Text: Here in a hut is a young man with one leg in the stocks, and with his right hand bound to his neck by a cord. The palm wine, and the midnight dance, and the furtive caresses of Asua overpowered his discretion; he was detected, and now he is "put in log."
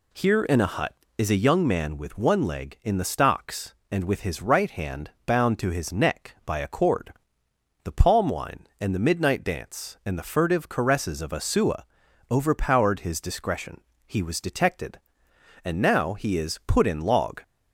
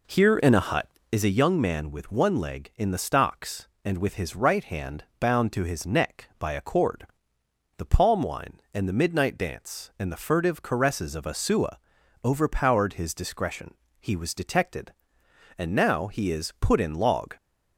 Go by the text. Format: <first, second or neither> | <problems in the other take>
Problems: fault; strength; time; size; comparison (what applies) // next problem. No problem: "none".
first | starts louder than the rest; until 1.2 s; 3.5 dB // pauses between "Asua" and "overpowered"; noticeable; at 11.7 s; 0.46 s long; noticeable in the first